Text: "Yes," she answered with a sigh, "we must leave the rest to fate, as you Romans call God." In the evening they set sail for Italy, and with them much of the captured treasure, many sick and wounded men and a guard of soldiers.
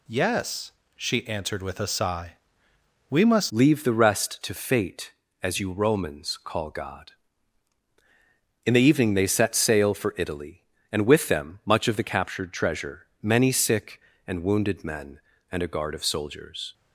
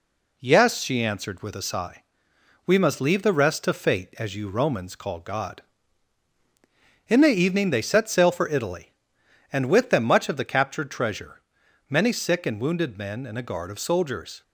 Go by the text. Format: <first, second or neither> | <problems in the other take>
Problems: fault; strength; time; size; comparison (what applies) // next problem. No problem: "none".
second | changes voice at "leave"; from 3.4 s on; 13.3 s long